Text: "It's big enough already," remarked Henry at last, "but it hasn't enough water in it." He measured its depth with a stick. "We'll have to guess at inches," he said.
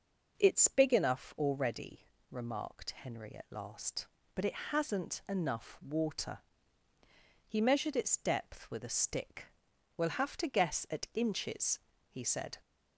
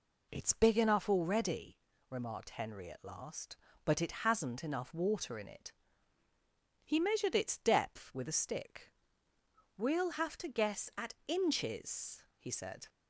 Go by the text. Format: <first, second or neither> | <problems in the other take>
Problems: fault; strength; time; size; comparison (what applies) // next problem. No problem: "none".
second | skips "in it"; at 6.9 s